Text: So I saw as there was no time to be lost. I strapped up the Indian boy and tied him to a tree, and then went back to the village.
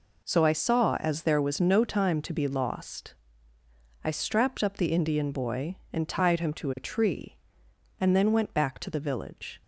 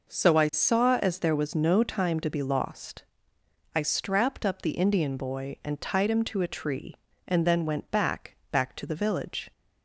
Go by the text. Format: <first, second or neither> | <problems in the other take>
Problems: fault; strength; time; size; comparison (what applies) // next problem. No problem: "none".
first | says "back" twice; at 8.5 s